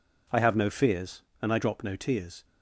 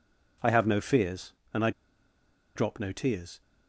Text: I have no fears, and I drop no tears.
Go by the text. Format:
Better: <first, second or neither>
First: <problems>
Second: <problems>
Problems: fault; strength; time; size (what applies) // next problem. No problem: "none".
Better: first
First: none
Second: pauses between "I" and "drop"; noticeable; at 1.7 s; 0.85 s long